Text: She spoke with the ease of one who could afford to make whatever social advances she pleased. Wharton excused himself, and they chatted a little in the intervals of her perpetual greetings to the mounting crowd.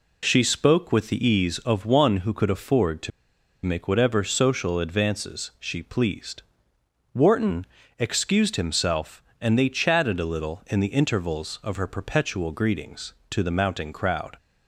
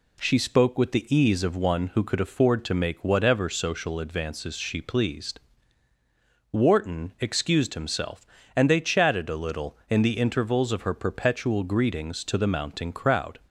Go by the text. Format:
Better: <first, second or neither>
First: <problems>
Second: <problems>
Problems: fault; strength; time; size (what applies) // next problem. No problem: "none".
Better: second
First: pauses between "to" and "make"; noticeable; at 3.1 s; 0.54 s long // pauses between "Wharton" and "excused"; slight; at 7.6 s; 0.32 s long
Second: none